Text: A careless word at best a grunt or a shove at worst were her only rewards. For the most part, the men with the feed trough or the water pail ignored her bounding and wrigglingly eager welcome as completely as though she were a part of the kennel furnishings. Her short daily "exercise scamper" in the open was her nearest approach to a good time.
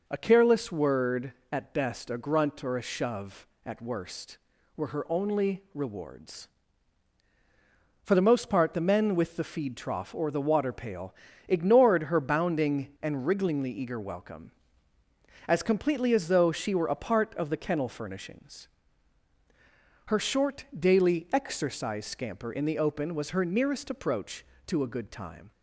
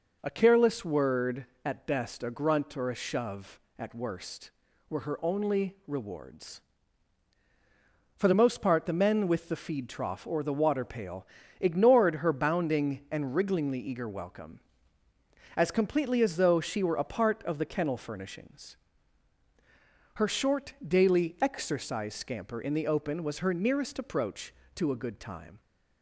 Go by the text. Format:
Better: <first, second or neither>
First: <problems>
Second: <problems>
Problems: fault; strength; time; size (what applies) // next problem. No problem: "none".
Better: neither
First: pauses between "pail" and "ignored"; slight; at 11.1 s; 0.36 s long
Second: pauses between "pail" and "ignored"; slight; at 11.2 s; 0.36 s long